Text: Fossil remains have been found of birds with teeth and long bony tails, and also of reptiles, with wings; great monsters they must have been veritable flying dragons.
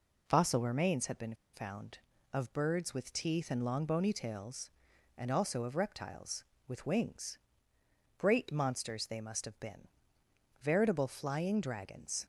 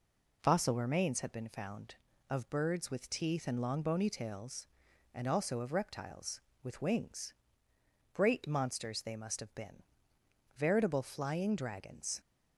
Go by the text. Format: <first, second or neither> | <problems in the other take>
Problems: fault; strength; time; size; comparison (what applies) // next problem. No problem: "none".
second | pauses between "been" and "found"; slight; at 1.3 s; 0.19 s long // pauses between "been" and "veritable"; noticeable; at 9.8 s; 0.72 s long; noticeable in the second